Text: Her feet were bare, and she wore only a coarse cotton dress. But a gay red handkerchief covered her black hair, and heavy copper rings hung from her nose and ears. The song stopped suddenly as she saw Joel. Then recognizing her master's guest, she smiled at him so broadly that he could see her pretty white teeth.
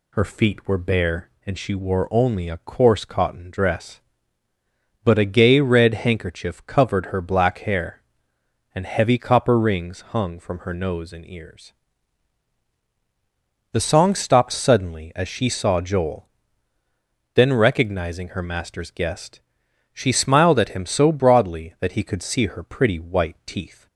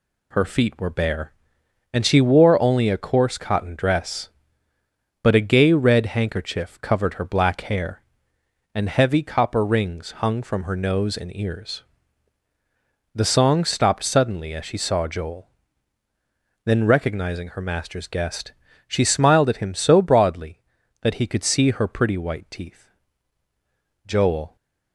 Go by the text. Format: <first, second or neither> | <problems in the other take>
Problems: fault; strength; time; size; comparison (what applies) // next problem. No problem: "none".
first | goes on to say "Joel"; from 24.0 s on; 0.50 s long